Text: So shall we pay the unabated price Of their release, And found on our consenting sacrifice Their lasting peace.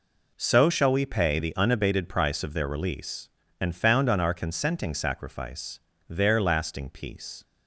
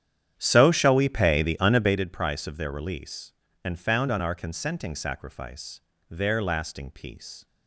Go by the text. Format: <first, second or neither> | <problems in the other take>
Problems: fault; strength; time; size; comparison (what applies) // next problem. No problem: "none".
first | starts louder than the rest; strong; until 2.0 s; 9.5 dB // pauses between "sacrifice" and "Their"; slight; at 5.8 s; 0.28 s long; slight in the first